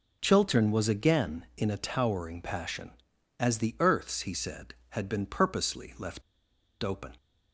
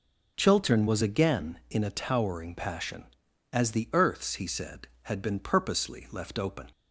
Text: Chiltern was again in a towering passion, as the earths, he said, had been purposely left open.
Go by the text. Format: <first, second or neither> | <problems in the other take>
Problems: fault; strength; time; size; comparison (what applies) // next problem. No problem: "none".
second | pauses between "left" and "open"; noticeable; at 6.2 s; 0.61 s long